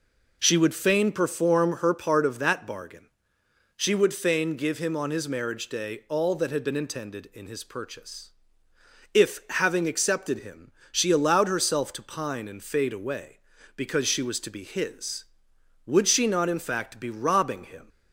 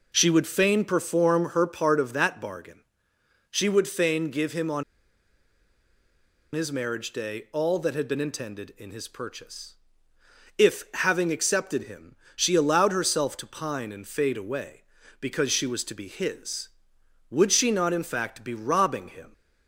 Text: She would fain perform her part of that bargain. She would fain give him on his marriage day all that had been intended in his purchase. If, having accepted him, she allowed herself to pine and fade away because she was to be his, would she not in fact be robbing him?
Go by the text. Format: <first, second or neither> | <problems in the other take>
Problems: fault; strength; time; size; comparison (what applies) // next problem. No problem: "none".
first | pauses between "on" and "his"; strong; at 4.8 s; 1.7 s long